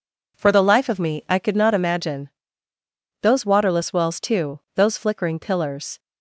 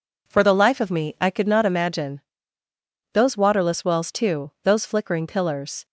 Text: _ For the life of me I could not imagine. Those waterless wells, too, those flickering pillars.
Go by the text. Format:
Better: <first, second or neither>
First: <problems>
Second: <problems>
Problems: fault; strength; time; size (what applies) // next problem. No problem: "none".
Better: neither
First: none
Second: none